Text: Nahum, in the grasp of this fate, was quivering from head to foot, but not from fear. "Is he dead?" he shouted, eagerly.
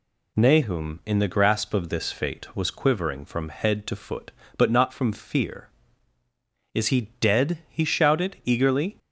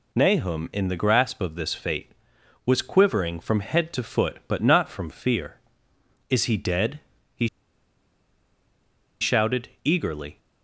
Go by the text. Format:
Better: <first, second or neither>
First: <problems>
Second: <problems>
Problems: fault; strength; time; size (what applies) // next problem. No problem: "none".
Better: first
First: none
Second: pauses between "he" and "shouted"; strong; at 7.4 s; 1.7 s long